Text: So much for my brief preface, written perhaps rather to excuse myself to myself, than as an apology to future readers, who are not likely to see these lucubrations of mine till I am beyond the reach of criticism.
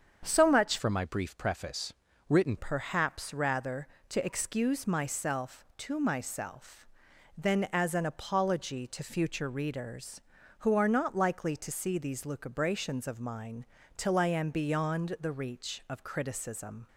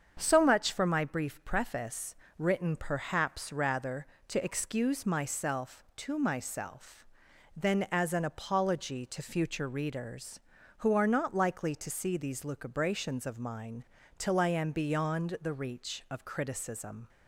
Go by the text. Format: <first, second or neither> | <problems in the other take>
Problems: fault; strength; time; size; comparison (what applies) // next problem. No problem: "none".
second | starts louder than the rest; strong; until 1.2 s; 7.5 dB; strong in the second // changes voice from "for" to "written"; from 0.7 to 2.5 s; 1.8 s long // pauses between "mine" and "till"; slight; at 13.6 s; 0.32 s long; slight in the second